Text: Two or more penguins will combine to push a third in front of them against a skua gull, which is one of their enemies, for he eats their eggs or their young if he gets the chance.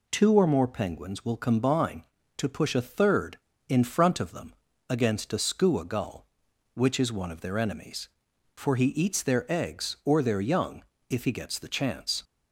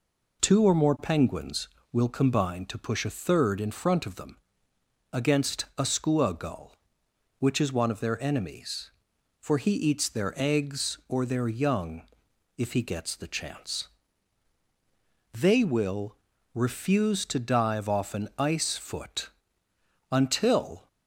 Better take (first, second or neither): first